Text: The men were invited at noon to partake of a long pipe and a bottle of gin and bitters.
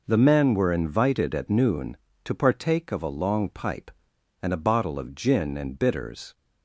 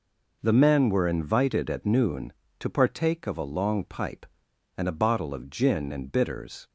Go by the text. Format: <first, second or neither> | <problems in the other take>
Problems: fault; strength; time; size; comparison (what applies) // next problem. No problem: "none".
neither | none